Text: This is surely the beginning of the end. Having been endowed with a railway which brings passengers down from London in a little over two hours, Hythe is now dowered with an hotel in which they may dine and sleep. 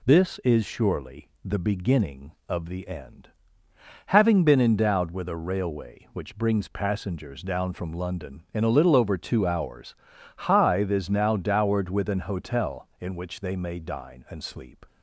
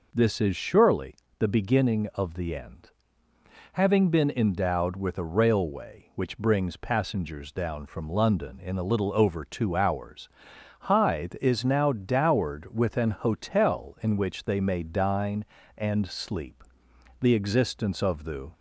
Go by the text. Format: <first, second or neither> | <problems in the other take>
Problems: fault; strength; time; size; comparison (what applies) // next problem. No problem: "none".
first | pauses between "surely" and "the"; slight; at 1.1 s; 0.20 s long; slight in the first // goes on to say "The existence of the"; from 17.2 s on; 1.3 s long